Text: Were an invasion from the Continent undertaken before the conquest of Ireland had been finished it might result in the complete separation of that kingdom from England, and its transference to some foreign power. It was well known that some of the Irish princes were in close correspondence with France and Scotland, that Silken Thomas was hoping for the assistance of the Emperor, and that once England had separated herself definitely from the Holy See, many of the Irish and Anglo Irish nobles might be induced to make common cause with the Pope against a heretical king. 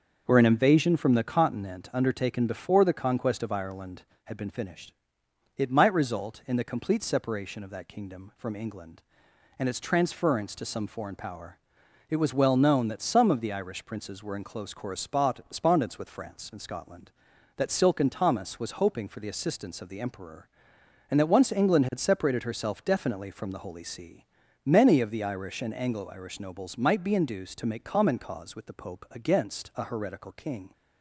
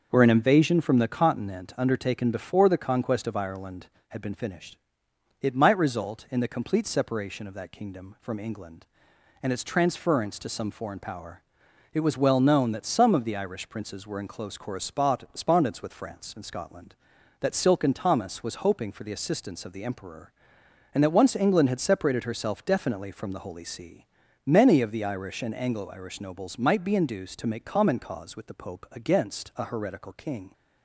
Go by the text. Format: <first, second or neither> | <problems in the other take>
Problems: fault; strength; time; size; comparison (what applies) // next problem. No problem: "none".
neither | starts louder than the rest; the same in both // pauses between "finished" and "it"; noticeable; the same in both